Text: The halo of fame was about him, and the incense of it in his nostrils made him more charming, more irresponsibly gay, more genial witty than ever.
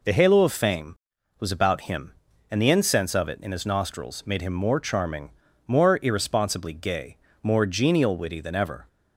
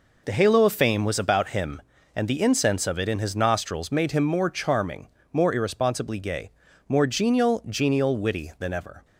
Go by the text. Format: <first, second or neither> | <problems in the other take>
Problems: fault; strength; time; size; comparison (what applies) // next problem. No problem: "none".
first | says "genial" twice; at 7.6 s